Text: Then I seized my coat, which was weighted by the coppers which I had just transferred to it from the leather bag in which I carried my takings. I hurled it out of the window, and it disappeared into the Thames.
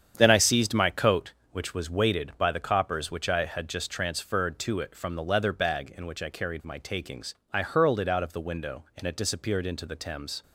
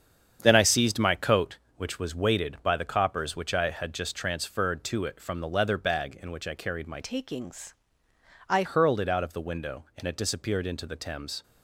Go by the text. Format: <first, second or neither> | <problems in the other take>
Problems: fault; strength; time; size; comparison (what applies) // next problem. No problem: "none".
first | starts louder than the rest; strong; until 1.4 s; 8 dB; strong in the first // changes voice from "takings" to "I"; from 7.0 to 8.6 s; 1.6 s long